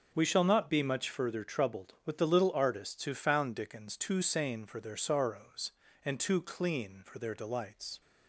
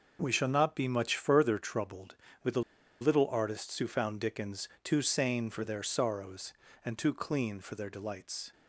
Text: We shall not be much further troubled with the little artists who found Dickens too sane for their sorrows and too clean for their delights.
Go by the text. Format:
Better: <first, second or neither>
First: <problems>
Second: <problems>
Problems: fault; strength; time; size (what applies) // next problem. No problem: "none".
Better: first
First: none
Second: pauses between "the" and "little"; at 2.6 s; 0.40 s long